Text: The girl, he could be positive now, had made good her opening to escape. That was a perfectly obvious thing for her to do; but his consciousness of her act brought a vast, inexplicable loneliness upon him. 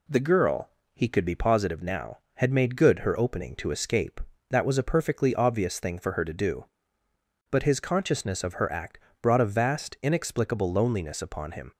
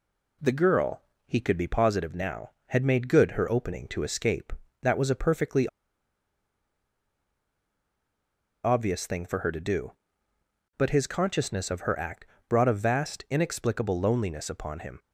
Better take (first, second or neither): first